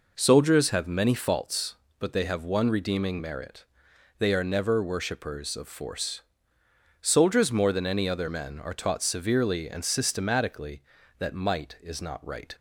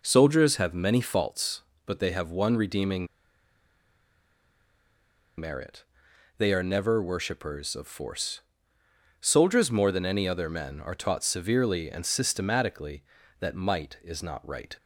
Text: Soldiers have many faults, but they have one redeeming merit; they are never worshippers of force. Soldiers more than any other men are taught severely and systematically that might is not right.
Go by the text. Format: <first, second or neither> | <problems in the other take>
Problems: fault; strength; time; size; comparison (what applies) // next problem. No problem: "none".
first | pauses between "redeeming" and "merit"; strong; at 3.0 s; 2.3 s long